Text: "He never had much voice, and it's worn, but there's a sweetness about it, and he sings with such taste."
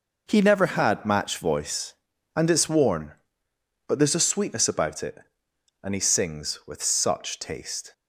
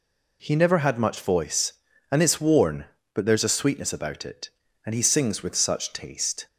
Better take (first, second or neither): second